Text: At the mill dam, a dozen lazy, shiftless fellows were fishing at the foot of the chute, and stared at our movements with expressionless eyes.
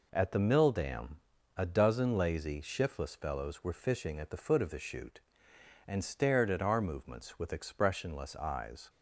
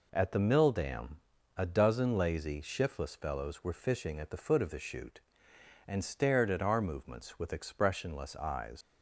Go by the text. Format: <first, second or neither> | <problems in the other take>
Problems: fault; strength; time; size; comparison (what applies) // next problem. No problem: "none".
first | leaves "eyes" unfinished; at 8.8 s; 85 ms